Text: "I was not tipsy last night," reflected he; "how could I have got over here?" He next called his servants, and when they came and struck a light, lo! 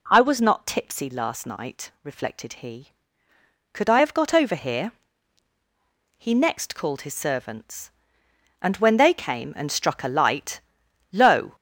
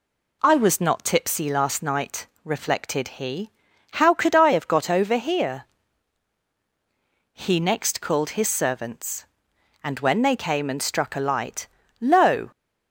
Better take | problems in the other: second | skips "how"; at 3.3 s

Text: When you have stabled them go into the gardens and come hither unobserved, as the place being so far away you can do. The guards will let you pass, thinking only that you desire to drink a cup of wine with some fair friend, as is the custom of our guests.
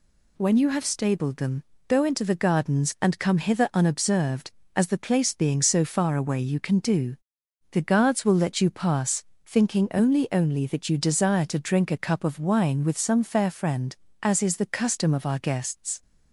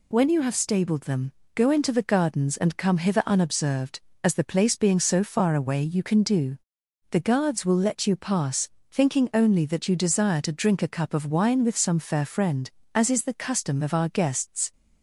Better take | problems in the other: second | pauses between "them" and "go"; slight; at 1.6 s; 0.24 s long; slight in the second // says "only" twice; at 10.3 s

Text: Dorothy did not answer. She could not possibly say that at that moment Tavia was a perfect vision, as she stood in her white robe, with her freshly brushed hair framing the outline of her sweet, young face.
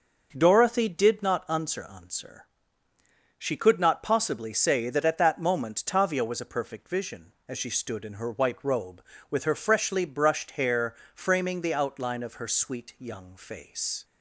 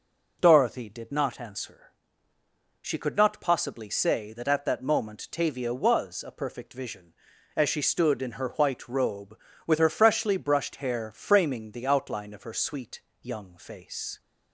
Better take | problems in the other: second | says "answer" twice; at 1.9 s // pauses between "hair" and "framing"; slight; at 10.9 s; 0.20 s long

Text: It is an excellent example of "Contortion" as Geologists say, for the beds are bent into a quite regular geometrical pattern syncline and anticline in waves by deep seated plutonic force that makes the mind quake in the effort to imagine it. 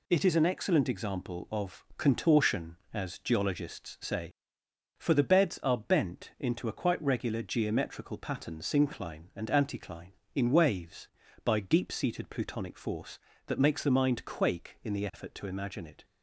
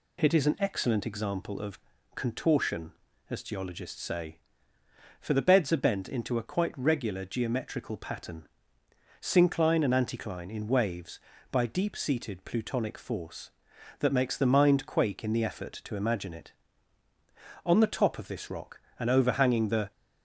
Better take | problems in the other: first | pauses between "of" and "Contortion"; slight; at 1.7 s; 0.34 s long // pauses between "pattern" and "syncline"; noticeable; at 8.4 s; 0.78 s long // goes on to say "On the top of this rock and overhanging the"; strong; from 17.6 s on; 2.2 s long

